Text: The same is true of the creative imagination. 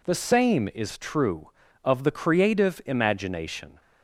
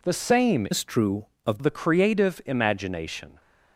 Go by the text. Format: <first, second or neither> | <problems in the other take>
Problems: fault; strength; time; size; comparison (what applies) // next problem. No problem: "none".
first | changes voice from "is" to "of"; from 0.7 to 1.5 s; 0.8 s long